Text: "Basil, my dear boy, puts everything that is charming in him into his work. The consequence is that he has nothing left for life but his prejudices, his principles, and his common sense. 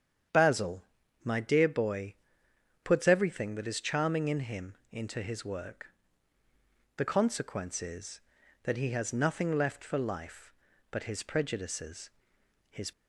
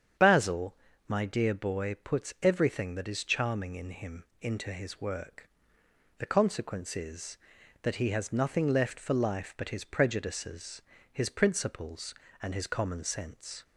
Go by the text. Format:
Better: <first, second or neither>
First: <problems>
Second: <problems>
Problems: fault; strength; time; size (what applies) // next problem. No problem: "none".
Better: second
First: starts louder than the rest; strong; until 1.7 s; 8 dB // pauses between "him" and "into"; slight; at 4.7 s; 0.16 s long // stops before "principles and his common sense"; at 12.9 s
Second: starts louder than the rest; strong; until 1.5 s; 8 dB // pauses between "him" and "into"; slight; at 4.2 s; 0.18 s long